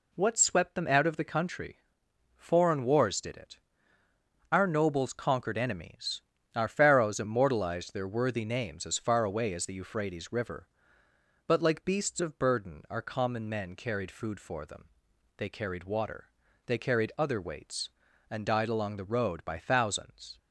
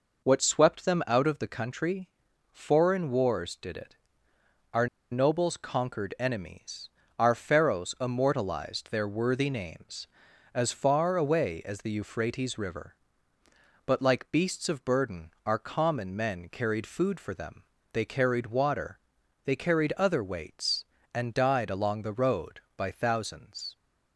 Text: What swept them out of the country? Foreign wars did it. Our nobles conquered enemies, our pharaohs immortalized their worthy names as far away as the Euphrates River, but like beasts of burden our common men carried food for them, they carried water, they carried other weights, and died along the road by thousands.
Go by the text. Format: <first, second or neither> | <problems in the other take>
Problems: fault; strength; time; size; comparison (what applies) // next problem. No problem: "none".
first | pauses between "Our" and "nobles"; slight; at 4.8 s; 0.25 s long // pauses between "burden" and "our"; slight; at 15.2 s; 0.16 s long